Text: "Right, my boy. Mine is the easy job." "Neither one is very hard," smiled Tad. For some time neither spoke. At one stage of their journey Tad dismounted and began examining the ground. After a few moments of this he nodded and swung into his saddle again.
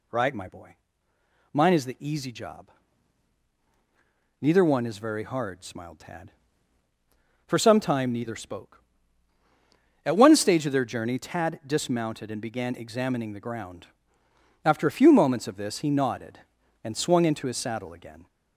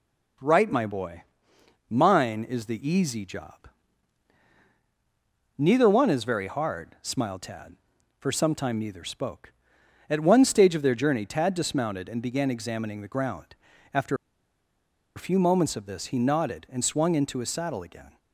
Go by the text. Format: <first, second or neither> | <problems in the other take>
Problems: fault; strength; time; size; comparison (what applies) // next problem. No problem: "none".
first | pauses between "After" and "a"; at 14.1 s; 1.0 s long